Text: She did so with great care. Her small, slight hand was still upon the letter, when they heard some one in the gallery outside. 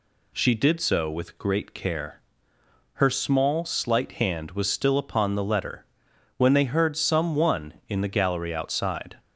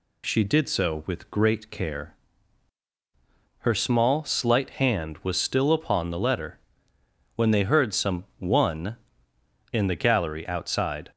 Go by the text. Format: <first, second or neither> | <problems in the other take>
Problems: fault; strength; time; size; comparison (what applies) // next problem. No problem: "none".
neither | none